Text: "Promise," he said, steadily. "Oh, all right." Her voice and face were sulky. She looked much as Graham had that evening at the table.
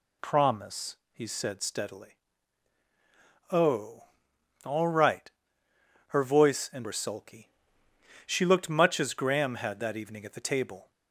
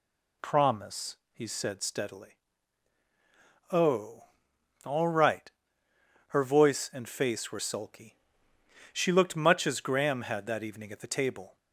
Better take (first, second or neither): second